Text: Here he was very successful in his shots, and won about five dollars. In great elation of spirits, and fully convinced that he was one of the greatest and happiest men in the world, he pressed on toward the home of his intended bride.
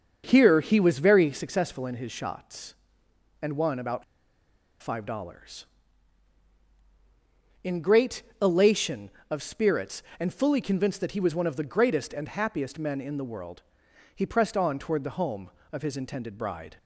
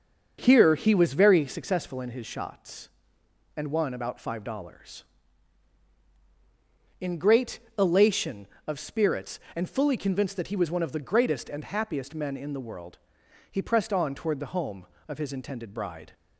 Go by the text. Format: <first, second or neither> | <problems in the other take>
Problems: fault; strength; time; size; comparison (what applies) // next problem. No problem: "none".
second | starts louder than the rest; until 1.2 s; 6.5 dB; also in the second // pauses between "about" and "five"; noticeable; at 4.0 s; 0.79 s long // pauses between "great" and "elation"; slight; at 8.2 s; 0.18 s long; slight in the second